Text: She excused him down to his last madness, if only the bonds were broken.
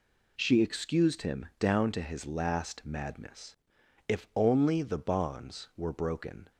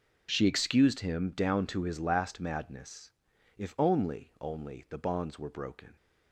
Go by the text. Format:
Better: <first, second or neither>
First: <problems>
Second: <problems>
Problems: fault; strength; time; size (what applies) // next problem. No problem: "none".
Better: first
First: none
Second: says "only" twice; at 4.3 s